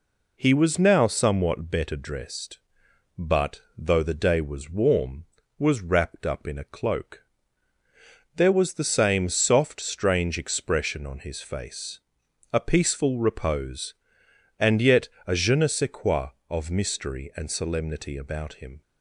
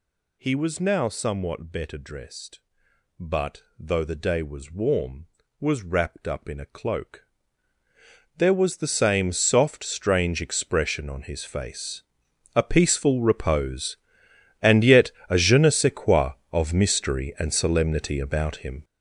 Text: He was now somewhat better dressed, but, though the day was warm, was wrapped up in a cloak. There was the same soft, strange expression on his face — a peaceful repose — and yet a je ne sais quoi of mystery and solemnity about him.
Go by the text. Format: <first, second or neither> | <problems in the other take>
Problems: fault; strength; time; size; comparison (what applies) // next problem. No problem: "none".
first | gets louder; strong; throughout; 10.5 dB // pauses between "yet" and "a"; slight; at 15.0 s; 0.18 s long; slight in the first